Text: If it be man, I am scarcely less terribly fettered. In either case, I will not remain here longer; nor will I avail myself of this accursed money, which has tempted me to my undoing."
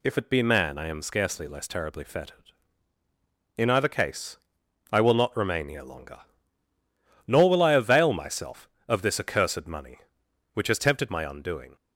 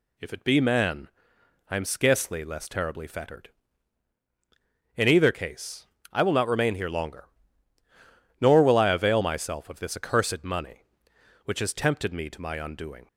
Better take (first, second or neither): second